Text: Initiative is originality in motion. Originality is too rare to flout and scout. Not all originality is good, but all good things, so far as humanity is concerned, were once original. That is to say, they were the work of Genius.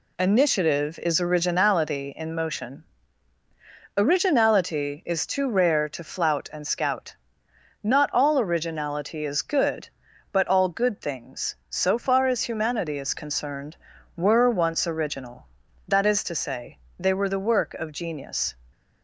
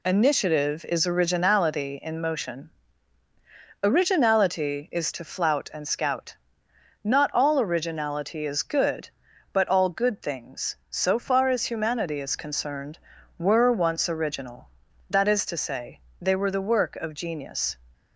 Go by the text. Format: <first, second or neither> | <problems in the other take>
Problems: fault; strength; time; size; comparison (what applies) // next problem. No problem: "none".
first | skips "too rare"; at 5.1 s